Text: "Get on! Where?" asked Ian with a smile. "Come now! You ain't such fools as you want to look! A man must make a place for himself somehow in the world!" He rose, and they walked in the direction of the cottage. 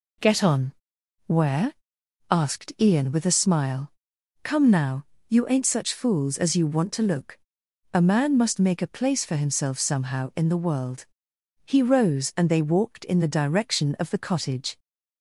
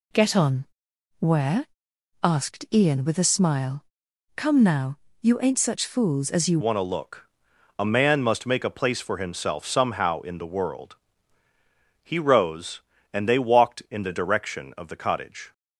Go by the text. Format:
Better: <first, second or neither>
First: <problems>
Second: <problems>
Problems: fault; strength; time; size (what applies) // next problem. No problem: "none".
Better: first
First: none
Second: changes voice at "want"; from 6.6 s on; 8.9 s long